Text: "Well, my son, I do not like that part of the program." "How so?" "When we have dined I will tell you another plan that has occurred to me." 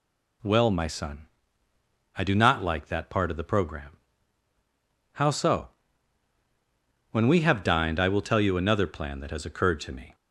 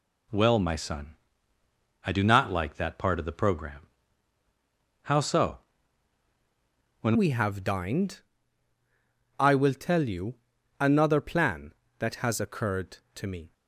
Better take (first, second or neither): first